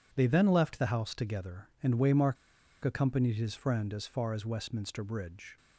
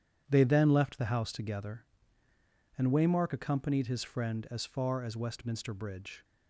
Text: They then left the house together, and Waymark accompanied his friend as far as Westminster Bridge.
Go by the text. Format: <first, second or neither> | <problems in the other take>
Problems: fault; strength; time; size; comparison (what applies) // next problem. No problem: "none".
second | pauses between "Waymark" and "accompanied"; noticeable; at 2.3 s; 0.48 s long